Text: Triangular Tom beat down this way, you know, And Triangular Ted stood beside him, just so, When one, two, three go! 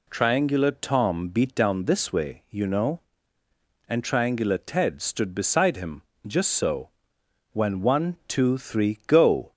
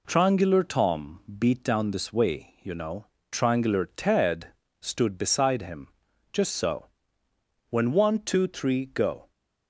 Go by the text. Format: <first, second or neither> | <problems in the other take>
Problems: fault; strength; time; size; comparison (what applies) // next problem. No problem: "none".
first | pauses between "Tom" and "beat"; slight; at 1.1 s; 0.22 s long // skips "And"; at 3.1 s // pauses between "Ted" and "stood"; slight; at 4.4 s; 0.32 s long